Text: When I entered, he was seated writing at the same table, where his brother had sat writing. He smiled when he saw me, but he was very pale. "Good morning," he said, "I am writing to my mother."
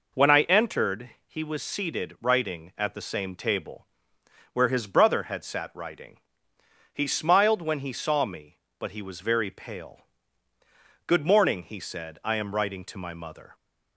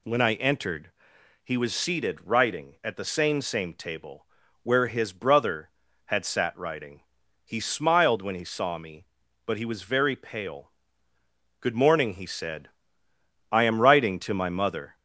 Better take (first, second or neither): first